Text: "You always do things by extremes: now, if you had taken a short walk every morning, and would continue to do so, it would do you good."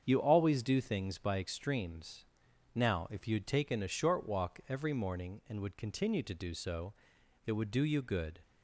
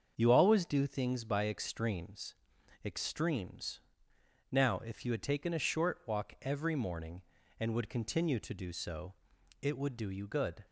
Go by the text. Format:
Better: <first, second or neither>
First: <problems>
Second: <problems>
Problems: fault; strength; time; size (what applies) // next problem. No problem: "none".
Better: first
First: starts louder than the rest; strong; until 1.0 s; 7.5 dB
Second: starts louder than the rest; until 1.1 s; 7 dB // says "extremes" twice; at 2.8 s